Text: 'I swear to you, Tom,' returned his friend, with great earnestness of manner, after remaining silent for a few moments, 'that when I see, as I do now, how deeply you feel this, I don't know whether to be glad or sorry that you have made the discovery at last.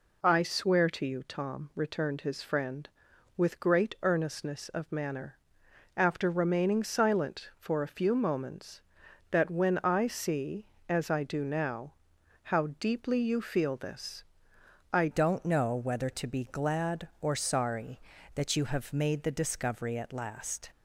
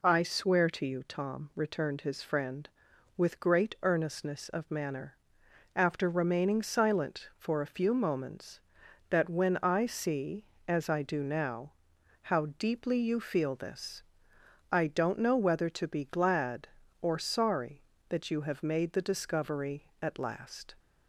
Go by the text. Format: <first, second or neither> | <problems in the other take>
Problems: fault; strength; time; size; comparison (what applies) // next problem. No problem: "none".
second | changes voice at "don't"; from 15.1 s on; 5.5 s long